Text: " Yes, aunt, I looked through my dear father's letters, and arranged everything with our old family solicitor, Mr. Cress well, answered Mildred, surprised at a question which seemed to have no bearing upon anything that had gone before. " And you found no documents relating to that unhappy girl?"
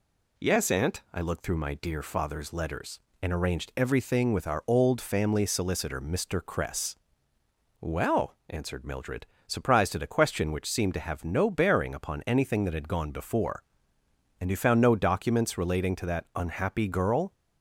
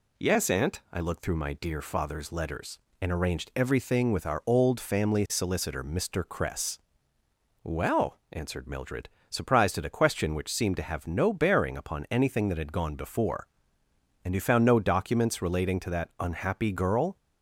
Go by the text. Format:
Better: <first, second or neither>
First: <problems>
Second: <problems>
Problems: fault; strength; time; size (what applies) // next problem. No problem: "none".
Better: neither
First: pauses between "Cress" and "well"; noticeable; at 6.9 s; 0.86 s long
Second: pauses between "Cress" and "well"; noticeable; at 6.7 s; 0.86 s long